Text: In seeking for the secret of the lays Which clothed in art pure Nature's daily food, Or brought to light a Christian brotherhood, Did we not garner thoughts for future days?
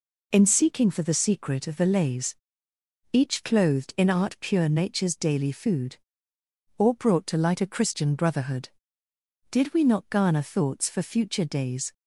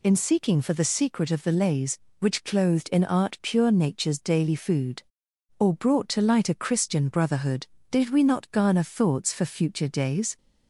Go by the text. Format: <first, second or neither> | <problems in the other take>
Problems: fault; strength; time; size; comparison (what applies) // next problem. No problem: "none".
second | says "Each" for "Which"; at 3.1 s